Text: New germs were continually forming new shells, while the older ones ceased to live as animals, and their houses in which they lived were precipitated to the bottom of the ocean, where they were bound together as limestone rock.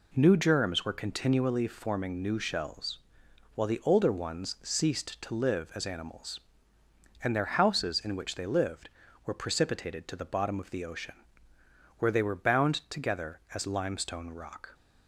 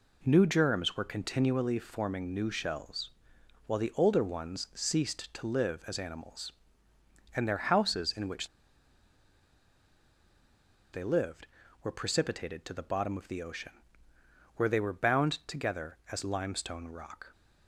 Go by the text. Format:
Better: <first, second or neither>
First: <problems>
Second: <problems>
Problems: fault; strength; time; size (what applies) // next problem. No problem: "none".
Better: first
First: pauses between "bound" and "together"; slight; at 12.7 s; 0.16 s long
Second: pauses between "which" and "they"; strong; at 8.4 s; 2.4 s long // pauses between "bound" and "together"; slight; at 15.3 s; 0.16 s long